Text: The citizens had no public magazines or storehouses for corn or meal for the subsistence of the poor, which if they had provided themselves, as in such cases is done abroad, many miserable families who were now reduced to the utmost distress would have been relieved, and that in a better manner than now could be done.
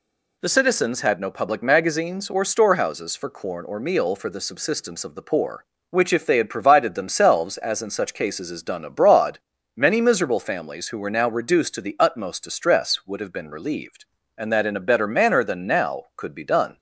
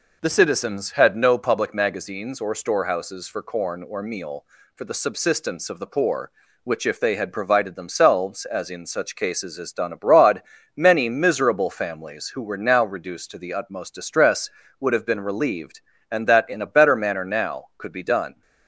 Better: first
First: none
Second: skips "than"; at 17.2 s

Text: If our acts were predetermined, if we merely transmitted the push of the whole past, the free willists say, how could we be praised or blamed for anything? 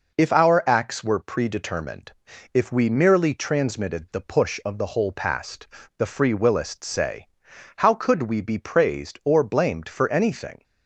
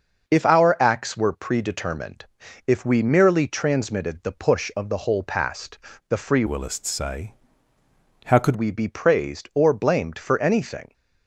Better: first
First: none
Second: starts louder than the rest; until 1.3 s; 6 dB // changes voice from "willists" to "could"; from 6.4 to 8.5 s; 2.1 s long

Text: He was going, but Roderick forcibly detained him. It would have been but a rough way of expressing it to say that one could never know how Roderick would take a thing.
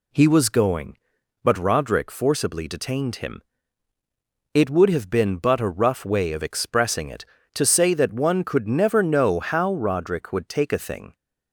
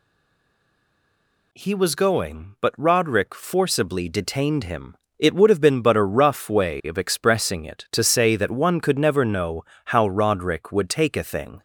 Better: first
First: none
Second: stays silent before the first word; noticeable; until 1.5 s; 1.5 s long // pauses between "know" and "how"; slight; at 9.6 s; 0.22 s long

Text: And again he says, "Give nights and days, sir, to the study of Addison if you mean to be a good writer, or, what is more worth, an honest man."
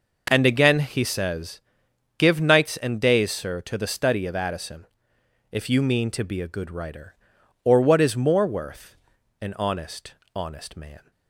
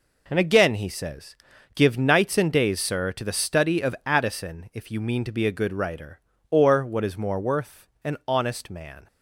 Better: second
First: pauses between "Addison" and "if"; noticeable; at 4.8 s; 0.66 s long // says "honest" twice; at 10.3 s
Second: none

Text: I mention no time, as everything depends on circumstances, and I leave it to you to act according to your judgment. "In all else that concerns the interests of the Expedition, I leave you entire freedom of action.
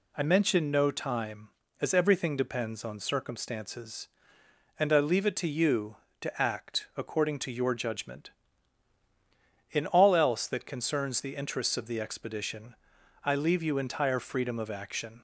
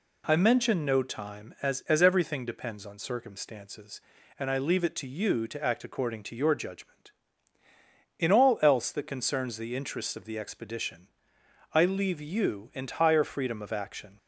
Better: first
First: none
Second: says "as" twice; at 1.8 s

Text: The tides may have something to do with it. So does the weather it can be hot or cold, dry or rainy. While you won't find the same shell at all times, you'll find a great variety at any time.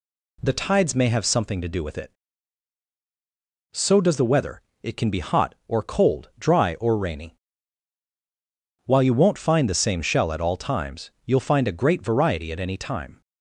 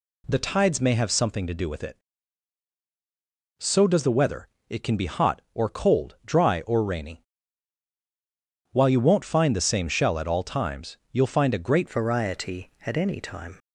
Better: first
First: pauses between "weather" and "it"; slight; at 4.6 s; 0.20 s long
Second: pauses between "weather" and "it"; slight; at 4.4 s; 0.20 s long // changes voice at "variety"; from 11.8 s on; 1.7 s long

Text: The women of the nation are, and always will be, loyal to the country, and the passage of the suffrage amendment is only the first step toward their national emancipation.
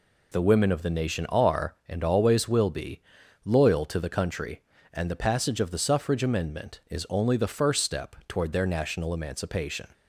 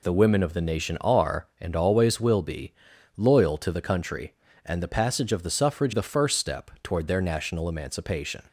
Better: first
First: none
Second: skips "amendment is only"; at 5.9 s

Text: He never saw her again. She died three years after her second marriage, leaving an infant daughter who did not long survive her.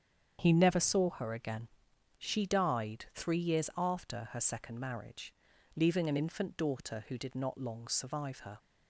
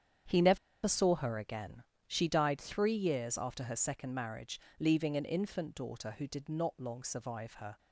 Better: first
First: starts louder than the rest; strong; until 1.4 s; 7.5 dB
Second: starts louder than the rest; strong; until 1.5 s; 8 dB // pauses between "never" and "saw"; slight; at 0.5 s; 0.27 s long

